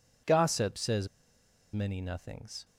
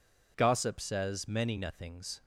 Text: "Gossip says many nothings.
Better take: second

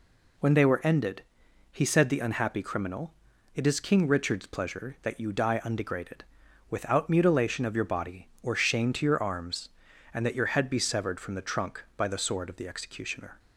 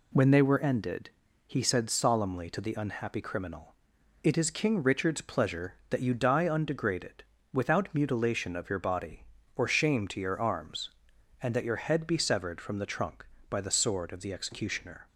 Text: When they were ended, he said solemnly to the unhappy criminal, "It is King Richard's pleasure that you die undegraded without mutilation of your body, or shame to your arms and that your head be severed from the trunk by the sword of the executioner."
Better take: second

